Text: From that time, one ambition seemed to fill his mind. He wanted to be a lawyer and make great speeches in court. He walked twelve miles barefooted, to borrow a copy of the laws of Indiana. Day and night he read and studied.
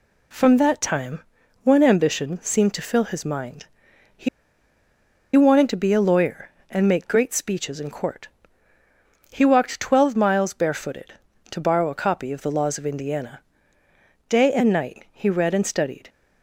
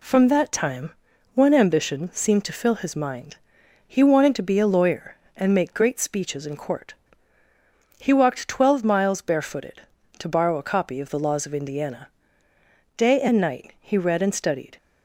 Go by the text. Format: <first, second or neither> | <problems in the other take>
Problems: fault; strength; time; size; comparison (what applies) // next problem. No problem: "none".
second | pauses between "He" and "wanted"; at 4.2 s; 1.0 s long